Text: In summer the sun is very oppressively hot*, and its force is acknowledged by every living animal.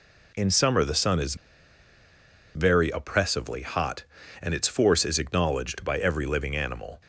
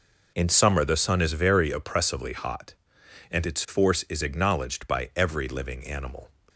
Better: second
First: pauses between "is" and "very"; at 1.3 s; 1.2 s long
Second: none

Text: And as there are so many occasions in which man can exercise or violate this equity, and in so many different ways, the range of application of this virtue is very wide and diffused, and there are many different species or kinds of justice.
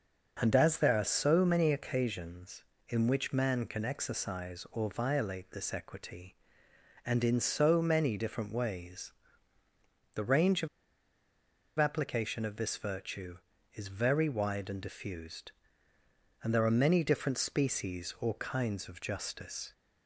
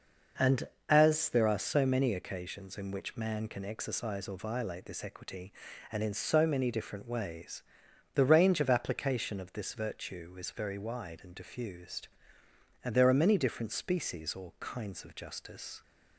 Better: second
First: starts louder than the rest; until 1.4 s; 6 dB // pauses between "of" and "application"; at 10.6 s; 1.1 s long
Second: none

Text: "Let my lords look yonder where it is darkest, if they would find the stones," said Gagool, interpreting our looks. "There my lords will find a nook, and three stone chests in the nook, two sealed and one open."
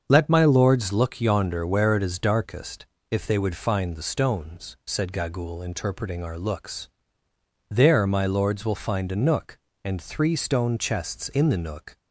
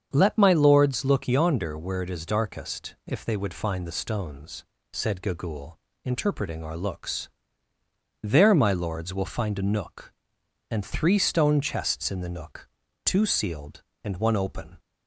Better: second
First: starts louder than the rest; until 1.1 s; 7 dB // stops before "two sealed and one open"; at 11.9 s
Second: starts louder than the rest; strong; until 1.1 s; 7 dB

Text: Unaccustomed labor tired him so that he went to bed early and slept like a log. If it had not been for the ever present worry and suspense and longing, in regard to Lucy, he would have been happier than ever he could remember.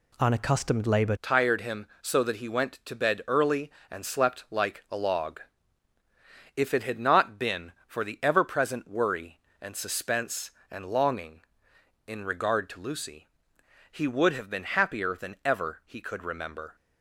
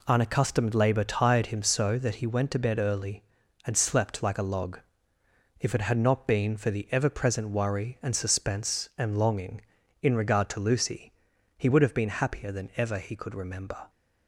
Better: second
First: changes voice at "tired"; from 1.2 s on; 15.5 s long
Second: none

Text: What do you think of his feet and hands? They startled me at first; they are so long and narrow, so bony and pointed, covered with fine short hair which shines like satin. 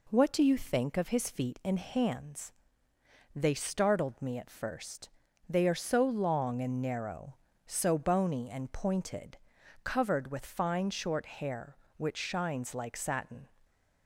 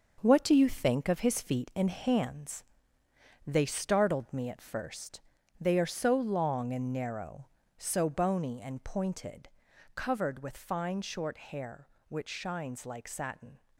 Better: first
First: none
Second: gets quieter; strong; throughout; 7.5 dB

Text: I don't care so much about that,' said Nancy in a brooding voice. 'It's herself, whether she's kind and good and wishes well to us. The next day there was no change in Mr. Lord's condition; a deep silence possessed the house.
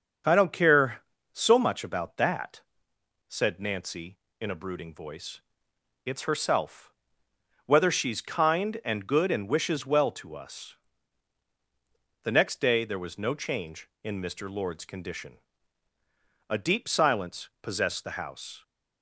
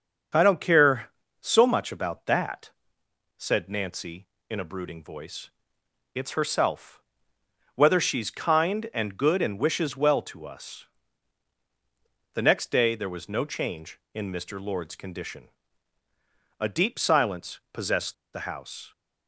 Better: first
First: starts louder than the rest; until 1.5 s; 7 dB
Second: starts louder than the rest; until 1.6 s; 7 dB // pauses between "possessed" and "the"; slight; at 18.1 s; 0.19 s long

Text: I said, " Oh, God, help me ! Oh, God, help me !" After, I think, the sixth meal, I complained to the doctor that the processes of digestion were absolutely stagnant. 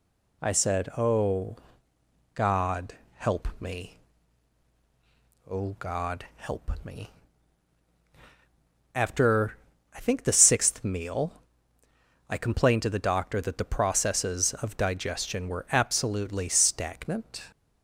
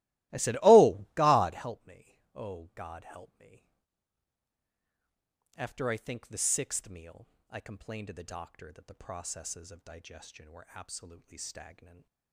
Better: first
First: none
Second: starts louder than the rest; strong; until 1.7 s; 17.5 dB // stays silent after the last word; slight; from 11.7 s on; 0.6 s long

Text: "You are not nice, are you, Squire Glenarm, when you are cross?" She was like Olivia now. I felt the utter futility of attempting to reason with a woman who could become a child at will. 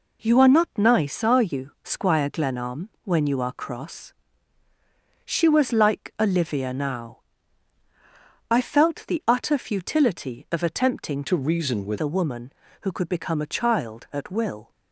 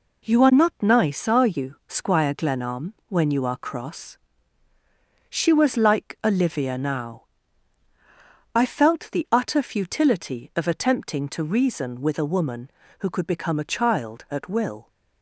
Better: second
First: changes voice from "to" to "with"; from 11.2 to 11.9 s; 0.7 s long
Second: none

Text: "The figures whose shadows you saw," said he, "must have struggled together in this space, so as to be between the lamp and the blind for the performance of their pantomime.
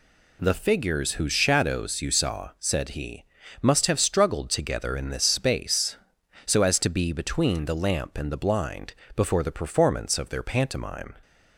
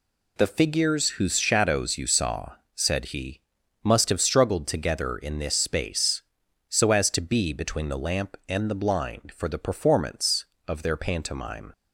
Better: second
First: says "before" for "for"; at 9.1 s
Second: none

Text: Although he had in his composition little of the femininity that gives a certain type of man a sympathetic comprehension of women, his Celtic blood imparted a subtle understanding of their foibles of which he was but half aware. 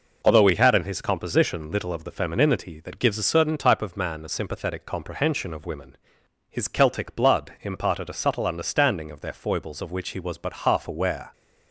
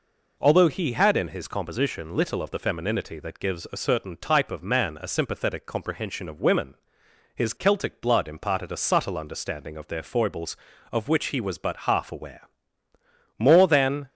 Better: first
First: none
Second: goes on to say "More than"; noticeable; from 13.3 s on; 0.72 s long

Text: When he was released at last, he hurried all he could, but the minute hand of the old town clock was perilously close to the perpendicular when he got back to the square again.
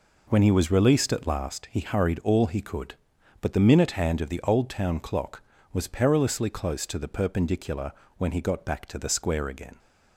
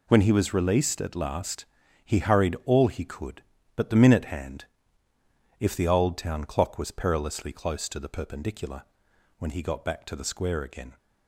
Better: first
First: pauses between "perpendicular" and "when"; slight; at 7.9 s; 0.26 s long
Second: says "if" for "of"; at 5.5 s // pauses between "perpendicular" and "when"; noticeable; at 8.8 s; 0.56 s long

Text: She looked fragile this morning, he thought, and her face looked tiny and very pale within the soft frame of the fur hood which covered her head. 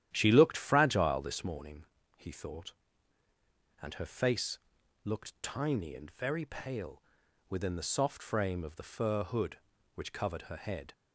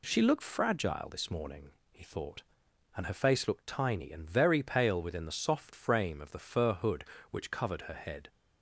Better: second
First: starts louder than the rest; strong; until 1.4 s; 11.5 dB // pauses between "face" and "looked"; noticeable; at 4.5 s; 0.48 s long // pauses between "pale" and "within"; noticeable; at 7.0 s; 0.46 s long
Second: none

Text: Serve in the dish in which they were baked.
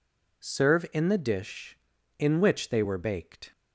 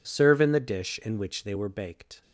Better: neither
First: none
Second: none

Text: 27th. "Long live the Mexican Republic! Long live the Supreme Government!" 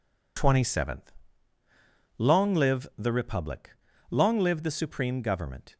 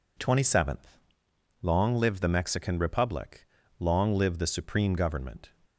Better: second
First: skips "Mexican"; at 3.1 s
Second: none

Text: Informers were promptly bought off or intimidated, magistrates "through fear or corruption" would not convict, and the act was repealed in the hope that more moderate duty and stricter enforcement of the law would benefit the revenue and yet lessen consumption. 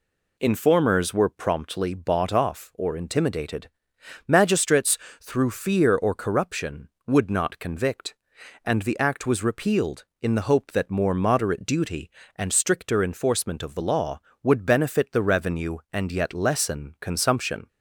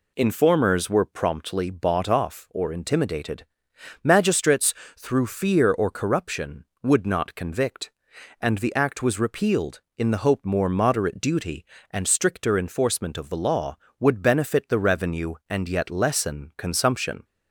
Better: first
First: pauses between "magistrates" and "through"; slight; at 4.9 s; 0.24 s long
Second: pauses between "magistrates" and "through"; slight; at 4.7 s; 0.24 s long // skips "that"; at 10.4 s

